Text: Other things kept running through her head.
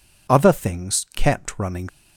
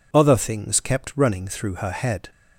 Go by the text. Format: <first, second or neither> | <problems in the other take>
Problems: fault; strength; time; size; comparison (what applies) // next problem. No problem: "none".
second | stops before "through her head"; at 1.8 s